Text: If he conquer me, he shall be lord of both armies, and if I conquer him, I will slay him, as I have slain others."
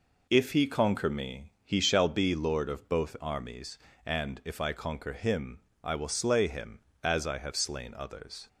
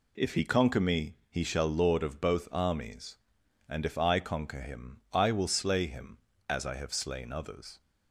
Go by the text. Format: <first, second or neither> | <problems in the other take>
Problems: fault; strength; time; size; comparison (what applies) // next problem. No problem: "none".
first | skips "be"; at 1.6 s